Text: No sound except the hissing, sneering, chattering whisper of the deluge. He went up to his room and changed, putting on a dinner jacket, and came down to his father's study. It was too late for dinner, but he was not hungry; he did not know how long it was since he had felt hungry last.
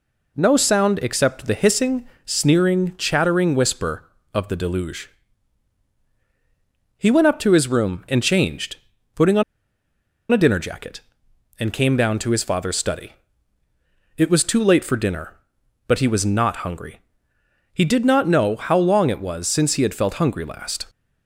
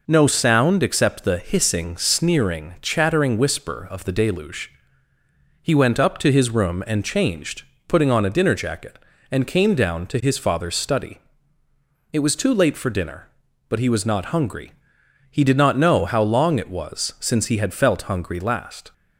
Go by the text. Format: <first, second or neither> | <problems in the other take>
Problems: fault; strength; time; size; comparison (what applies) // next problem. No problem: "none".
second | pauses between "on" and "a"; noticeable; at 9.4 s; 0.89 s long